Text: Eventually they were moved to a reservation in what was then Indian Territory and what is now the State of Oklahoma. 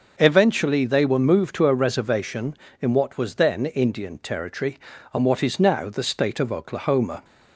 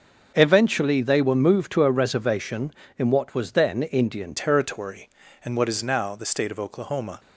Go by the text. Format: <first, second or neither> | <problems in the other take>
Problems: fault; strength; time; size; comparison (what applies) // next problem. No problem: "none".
first | starts louder than the rest; until 1.3 s; 6.5 dB; noticeable in the first // changes voice at "Territory"; from 4.3 s on; 2.8 s long